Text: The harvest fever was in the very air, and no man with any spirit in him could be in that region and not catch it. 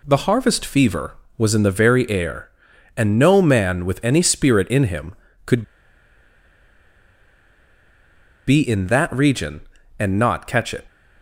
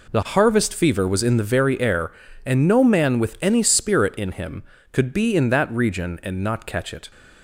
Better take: second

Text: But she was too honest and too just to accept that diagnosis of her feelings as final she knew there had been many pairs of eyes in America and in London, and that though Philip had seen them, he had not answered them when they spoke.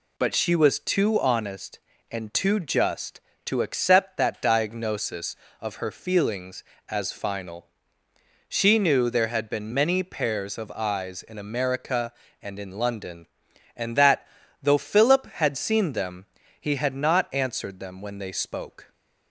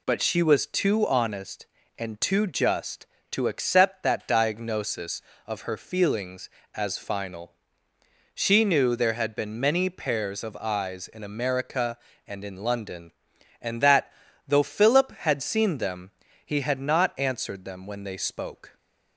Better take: neither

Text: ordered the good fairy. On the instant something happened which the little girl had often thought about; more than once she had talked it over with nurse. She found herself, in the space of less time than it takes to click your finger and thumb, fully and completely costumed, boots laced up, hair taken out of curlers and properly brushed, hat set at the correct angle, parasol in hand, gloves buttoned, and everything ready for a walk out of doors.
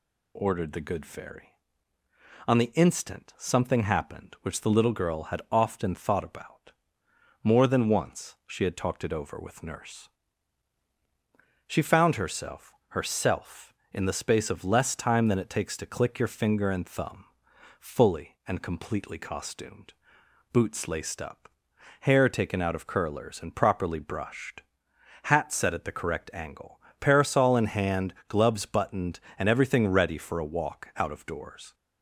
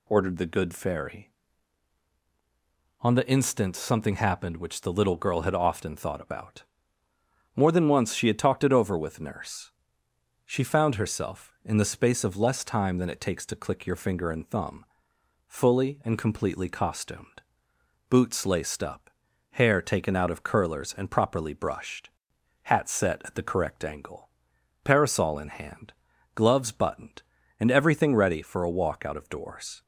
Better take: second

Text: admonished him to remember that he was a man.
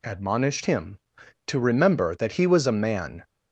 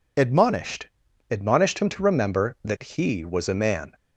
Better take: first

